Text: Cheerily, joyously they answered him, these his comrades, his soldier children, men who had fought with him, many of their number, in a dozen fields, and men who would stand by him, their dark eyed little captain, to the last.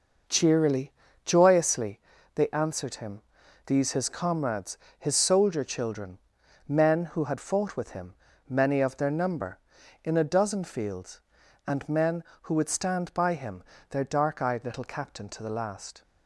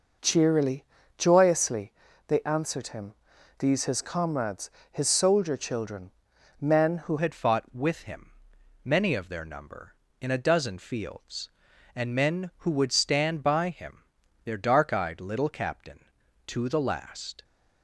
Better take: first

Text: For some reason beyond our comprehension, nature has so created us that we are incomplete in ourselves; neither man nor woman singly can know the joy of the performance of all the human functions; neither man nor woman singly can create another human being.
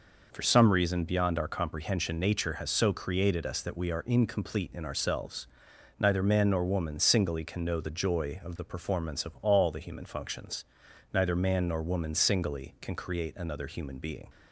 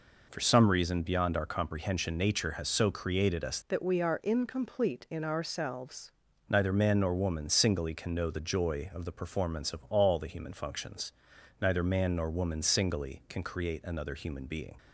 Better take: first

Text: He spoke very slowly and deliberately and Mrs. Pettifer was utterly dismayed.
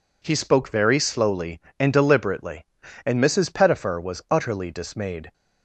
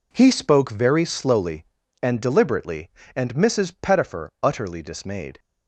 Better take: first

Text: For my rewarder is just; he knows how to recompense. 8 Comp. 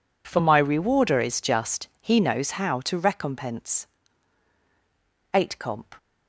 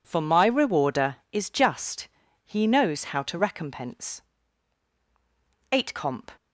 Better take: neither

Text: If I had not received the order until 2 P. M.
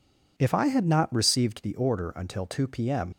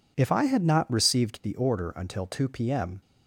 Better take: second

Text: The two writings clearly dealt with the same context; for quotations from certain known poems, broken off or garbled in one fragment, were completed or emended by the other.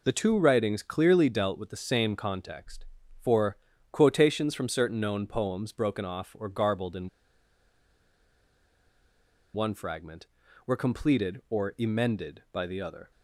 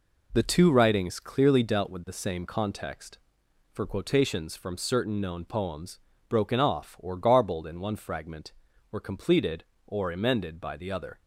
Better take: second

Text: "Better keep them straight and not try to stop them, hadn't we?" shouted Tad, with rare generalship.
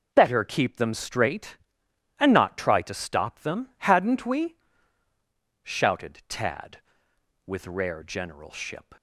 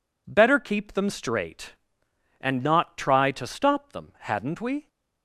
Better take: first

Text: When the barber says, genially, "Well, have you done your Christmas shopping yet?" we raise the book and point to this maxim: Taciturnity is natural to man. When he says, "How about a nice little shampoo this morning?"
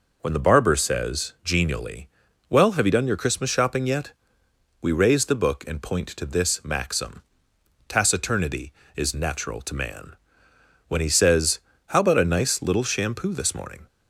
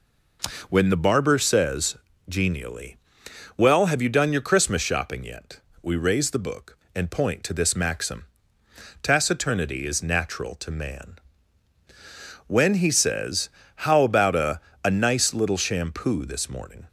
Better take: first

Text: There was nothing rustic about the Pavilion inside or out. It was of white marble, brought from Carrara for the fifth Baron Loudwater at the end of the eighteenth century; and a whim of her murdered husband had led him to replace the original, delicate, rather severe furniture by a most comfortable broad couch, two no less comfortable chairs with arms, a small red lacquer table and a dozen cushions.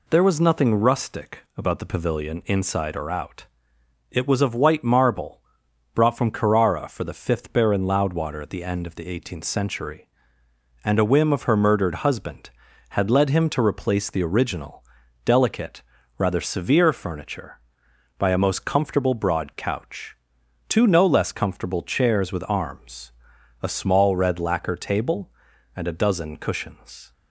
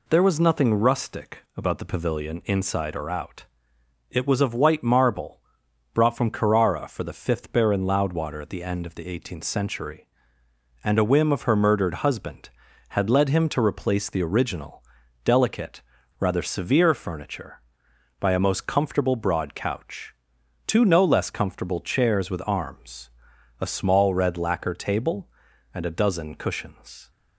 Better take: neither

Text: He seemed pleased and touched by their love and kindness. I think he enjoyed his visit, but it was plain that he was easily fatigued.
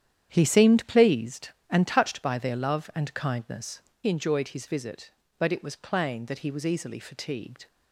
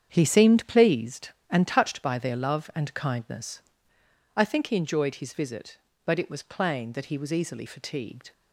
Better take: second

